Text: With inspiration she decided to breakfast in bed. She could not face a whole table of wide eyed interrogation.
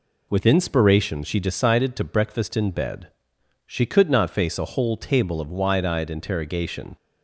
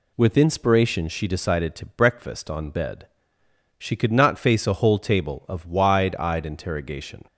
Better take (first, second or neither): first